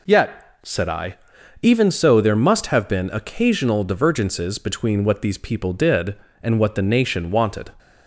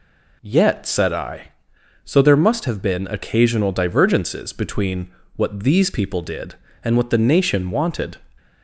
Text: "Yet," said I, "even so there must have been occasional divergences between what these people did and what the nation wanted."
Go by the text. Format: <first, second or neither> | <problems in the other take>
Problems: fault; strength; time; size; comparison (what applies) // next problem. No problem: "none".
first | skips "even"; at 1.7 s // pauses between "between" and "what"; slight; at 5.0 s; 0.26 s long